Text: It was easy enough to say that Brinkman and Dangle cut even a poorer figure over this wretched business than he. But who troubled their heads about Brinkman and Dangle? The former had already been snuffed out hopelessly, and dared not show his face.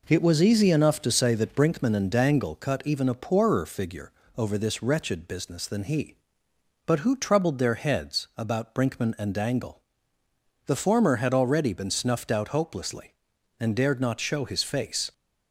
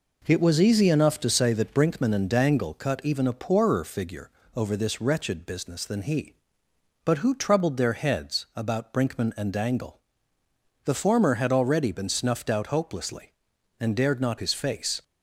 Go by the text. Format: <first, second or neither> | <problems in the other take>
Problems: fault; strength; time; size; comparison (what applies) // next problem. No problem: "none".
first | pauses between "figure" and "over"; slight; at 4.3 s; 0.24 s long; slight in the first // skips "show"; at 14.3 s